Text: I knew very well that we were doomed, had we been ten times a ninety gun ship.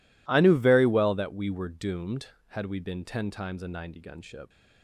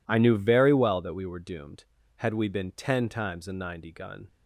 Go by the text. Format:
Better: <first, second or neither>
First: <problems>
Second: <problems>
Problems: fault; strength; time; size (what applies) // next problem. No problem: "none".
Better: first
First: none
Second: stops before "ship"; at 4.2 s